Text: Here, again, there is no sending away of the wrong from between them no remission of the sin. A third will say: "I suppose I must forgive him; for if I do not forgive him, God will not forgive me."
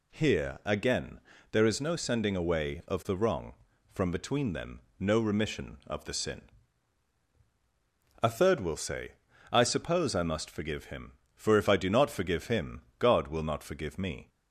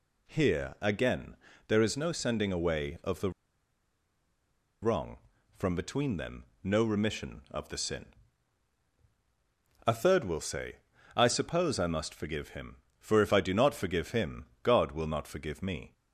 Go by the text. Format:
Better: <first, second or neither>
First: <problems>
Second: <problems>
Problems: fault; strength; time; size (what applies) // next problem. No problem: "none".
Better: first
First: pauses between "them" and "no"; slight; at 4.8 s; 0.18 s long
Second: pauses between "the" and "wrong"; strong; at 3.3 s; 1.5 s long // pauses between "them" and "no"; slight; at 6.4 s; 0.18 s long